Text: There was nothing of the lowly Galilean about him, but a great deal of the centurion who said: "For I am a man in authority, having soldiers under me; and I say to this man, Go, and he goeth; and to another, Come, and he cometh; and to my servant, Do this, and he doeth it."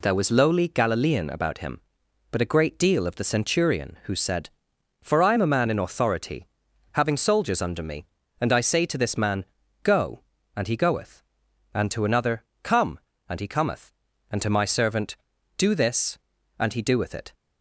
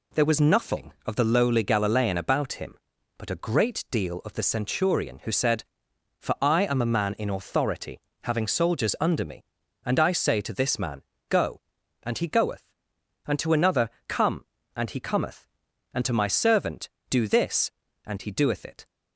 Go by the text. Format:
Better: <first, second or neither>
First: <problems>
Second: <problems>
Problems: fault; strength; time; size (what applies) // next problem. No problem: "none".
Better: second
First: skips "nothing of the"; at 0.3 s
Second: none